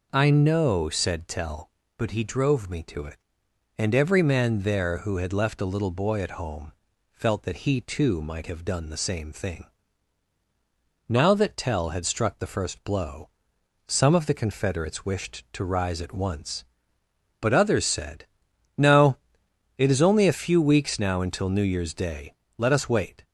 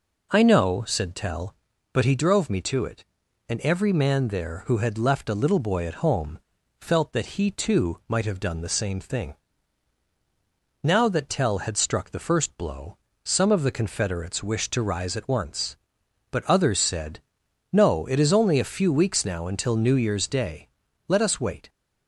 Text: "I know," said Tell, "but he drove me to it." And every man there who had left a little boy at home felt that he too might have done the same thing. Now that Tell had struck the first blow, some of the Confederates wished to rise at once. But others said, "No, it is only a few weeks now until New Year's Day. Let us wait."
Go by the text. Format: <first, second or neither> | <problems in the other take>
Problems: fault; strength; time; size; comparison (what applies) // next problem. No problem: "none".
neither | pauses between "home" and "felt"; the same in both